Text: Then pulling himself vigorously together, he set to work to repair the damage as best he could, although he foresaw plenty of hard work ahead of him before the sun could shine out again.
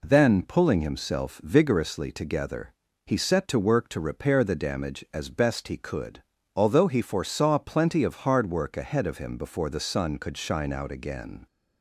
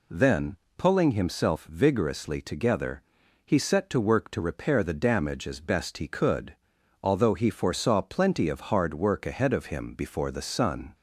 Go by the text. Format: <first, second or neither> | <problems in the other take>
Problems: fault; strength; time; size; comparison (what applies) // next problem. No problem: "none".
first | pauses between "Then" and "pulling"; slight; at 0.5 s; 0.20 s long // stops before "could shine out again"; at 10.9 s